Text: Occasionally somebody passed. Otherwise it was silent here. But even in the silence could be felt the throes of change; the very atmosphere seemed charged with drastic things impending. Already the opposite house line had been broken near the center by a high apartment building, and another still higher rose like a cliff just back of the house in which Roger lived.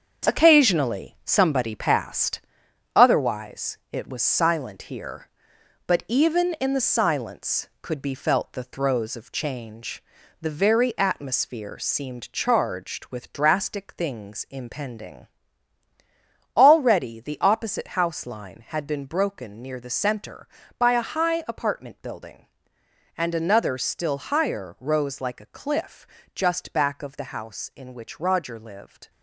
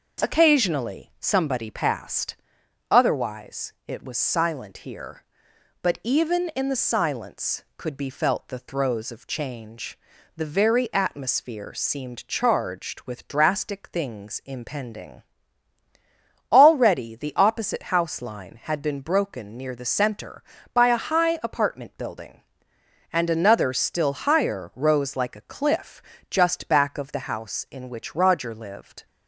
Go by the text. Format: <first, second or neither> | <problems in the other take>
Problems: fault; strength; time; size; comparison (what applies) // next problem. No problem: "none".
second | gets quieter; throughout; 7 dB // pauses between "cliff" and "just"; slight; at 26.0 s; 0.28 s long; slight in the second